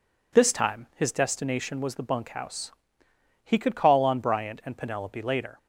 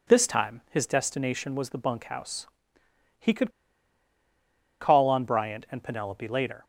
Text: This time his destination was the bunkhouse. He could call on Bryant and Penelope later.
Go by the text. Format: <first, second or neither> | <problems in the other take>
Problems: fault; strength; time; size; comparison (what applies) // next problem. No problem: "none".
first | pauses between "could" and "call"; strong; at 3.5 s; 1.3 s long